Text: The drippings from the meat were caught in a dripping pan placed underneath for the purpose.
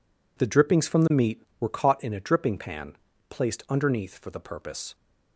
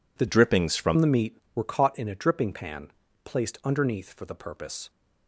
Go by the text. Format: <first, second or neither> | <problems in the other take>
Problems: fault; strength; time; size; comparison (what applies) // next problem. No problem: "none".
first | changes voice from "drippings" to "from"; from 0.2 to 0.9 s; 0.7 s long // pauses between "pan" and "placed"; slight; at 2.9 s; 0.32 s long; slight in the first